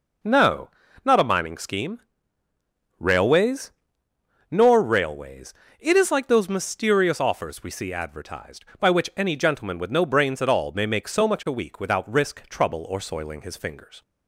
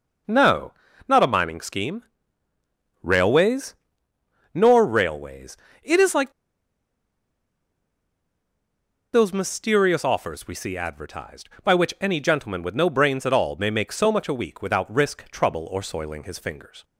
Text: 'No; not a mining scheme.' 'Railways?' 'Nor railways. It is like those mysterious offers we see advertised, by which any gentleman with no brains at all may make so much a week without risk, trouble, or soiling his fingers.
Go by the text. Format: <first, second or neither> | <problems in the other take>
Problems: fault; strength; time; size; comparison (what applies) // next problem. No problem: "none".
first | pauses between "like" and "those"; strong; at 6.3 s; 2.8 s long